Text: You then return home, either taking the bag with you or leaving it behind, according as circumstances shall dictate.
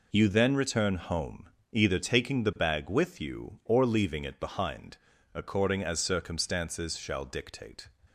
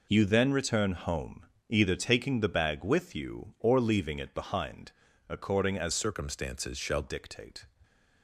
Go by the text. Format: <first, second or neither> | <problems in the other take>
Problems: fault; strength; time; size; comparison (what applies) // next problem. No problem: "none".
first | changes voice from "circumstances" to "shall"; from 5.9 to 7.0 s; 1.1 s long